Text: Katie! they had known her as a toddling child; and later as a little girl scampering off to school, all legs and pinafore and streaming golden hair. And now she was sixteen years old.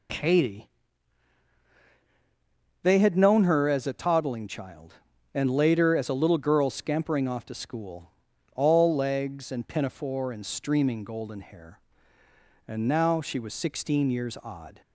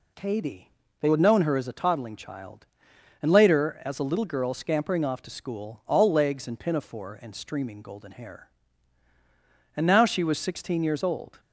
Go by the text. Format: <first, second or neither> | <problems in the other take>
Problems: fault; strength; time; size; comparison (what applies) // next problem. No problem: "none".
second | says "odd" for "old"; at 14.4 s